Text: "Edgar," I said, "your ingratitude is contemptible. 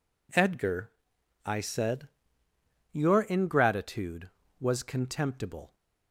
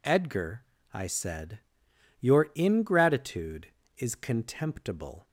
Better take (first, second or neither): second